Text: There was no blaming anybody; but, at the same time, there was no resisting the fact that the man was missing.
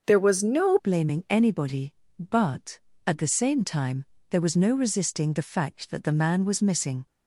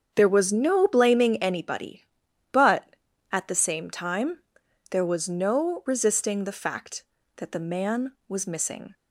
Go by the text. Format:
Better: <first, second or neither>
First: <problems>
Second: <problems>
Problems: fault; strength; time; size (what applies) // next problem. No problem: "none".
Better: second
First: starts louder than the rest; noticeable; until 1.0 s; 6 dB // changes voice at "blaming"; from 0.7 s on; 6.3 s long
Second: starts louder than the rest; strong; until 1.1 s; 7.5 dB